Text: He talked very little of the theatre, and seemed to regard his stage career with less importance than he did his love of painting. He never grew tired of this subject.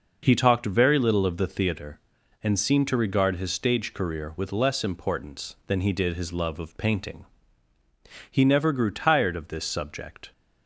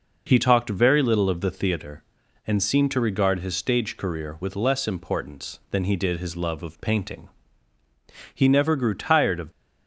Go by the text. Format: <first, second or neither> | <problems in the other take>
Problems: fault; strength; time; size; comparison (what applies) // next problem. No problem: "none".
first | stops before "this subject"; at 9.5 s